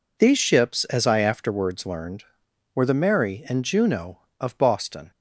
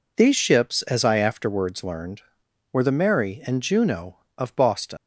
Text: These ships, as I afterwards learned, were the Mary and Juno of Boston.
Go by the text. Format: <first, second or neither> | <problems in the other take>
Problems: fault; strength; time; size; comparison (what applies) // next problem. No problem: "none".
first | leaves "Boston" unfinished; at 4.9 s; 110 ms